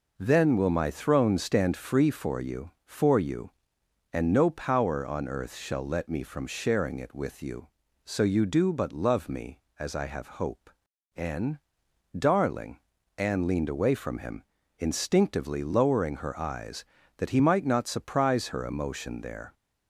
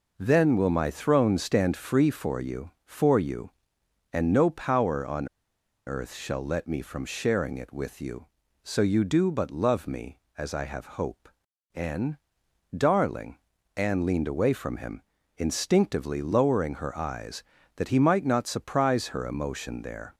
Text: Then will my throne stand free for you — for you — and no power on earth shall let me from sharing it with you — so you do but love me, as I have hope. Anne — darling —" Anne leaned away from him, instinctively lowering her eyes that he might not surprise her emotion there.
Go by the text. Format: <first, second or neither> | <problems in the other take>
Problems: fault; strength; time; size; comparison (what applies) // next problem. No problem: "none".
first | pauses between "on" and "earth"; noticeable; at 5.2 s; 0.58 s long